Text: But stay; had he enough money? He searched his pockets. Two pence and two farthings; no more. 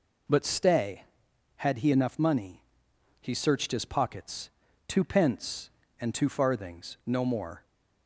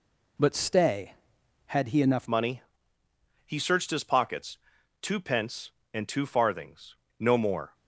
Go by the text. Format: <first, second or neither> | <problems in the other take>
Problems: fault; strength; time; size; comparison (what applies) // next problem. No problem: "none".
first | changes voice at "money"; from 2.2 s on; 5.5 s long